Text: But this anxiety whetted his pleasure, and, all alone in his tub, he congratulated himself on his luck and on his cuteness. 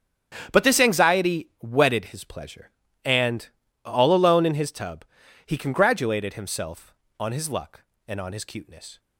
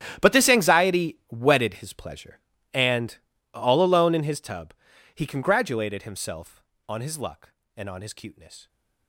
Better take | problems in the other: first | gets quieter; strong; throughout; 17.5 dB // starts louder than the rest; strong; until 1.3 s; 11 dB; strong in the first

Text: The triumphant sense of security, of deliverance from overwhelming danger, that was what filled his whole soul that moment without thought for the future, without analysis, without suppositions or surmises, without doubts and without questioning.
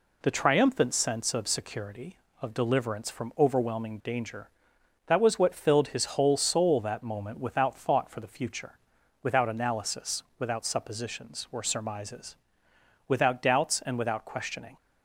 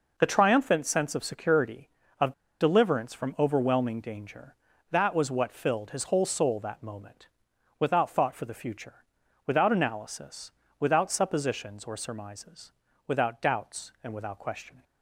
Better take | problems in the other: first | pauses between "of" and "deliverance"; slight; at 2.3 s; 0.27 s long // pauses between "moment" and "without"; noticeable; at 7.2 s; 0.52 s long

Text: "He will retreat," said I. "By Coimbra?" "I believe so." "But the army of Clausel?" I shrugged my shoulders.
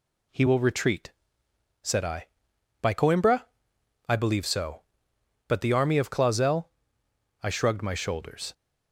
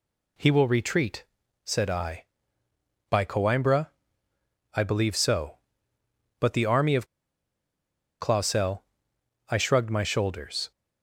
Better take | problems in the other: first | pauses between "of" and "Clausel"; at 7.0 s; 1.1 s long

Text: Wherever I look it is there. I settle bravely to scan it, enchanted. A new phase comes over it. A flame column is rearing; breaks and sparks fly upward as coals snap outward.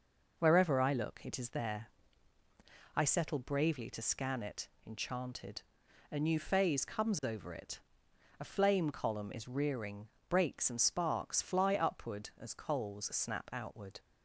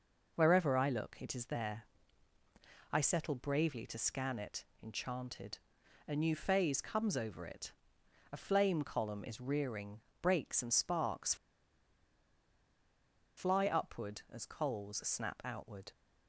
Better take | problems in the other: first | pauses between "sparks" and "fly"; strong; at 11.3 s; 2.0 s long

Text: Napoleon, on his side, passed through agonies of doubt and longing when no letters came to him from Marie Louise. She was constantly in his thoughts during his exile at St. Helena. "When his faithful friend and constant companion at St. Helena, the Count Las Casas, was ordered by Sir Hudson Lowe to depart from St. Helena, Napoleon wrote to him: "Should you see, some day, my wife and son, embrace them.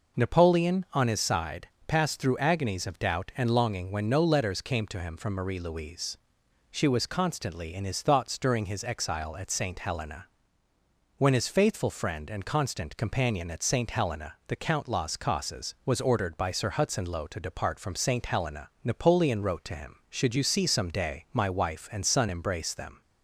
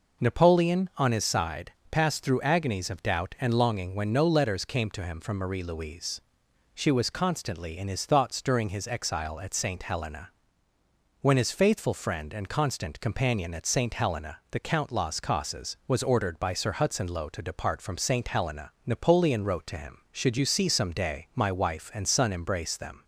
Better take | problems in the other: neither | none

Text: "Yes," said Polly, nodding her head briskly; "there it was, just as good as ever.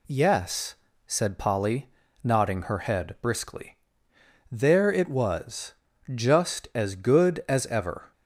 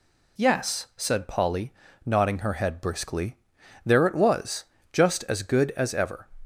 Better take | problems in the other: neither | none

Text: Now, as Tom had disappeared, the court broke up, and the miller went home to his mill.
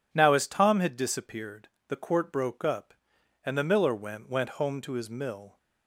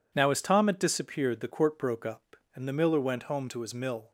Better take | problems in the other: second | says "went" twice; at 4.2 s

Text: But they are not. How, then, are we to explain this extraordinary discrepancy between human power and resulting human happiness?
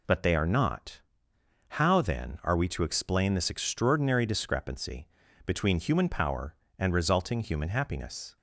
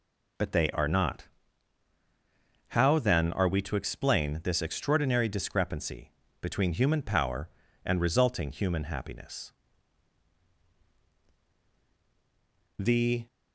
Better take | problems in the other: first | pauses between "discrepancy" and "between"; slight; at 6.1 s; 0.30 s long; slight in the first // goes on to say "The"; slight; from 12.7 s on; 0.46 s long

